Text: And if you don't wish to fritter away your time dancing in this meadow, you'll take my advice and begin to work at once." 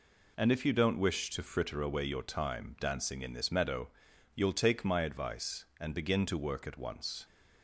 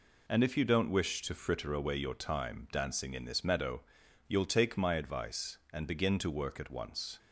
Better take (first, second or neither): neither